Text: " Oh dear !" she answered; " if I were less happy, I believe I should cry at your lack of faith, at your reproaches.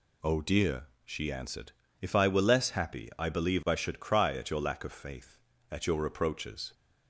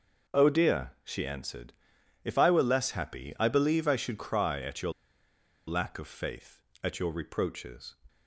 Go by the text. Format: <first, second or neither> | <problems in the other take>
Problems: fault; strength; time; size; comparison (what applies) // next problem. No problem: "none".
first | pauses between "your" and "lack"; noticeable; at 4.9 s; 0.76 s long